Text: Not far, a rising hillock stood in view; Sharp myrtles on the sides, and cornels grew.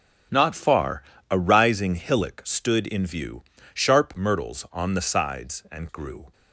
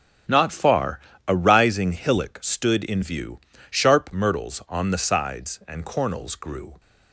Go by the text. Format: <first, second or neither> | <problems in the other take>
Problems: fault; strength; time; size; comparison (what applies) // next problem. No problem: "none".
second | starts louder than the rest; strong; until 1.6 s; 8.5 dB; strong in the second // skips "cornels"; at 5.8 s